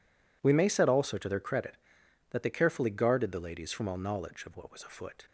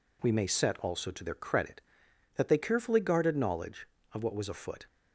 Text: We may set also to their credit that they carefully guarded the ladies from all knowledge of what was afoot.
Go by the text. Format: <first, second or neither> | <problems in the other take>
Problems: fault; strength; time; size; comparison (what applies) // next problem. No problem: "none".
first | skips "the ladies from all"; at 3.3 s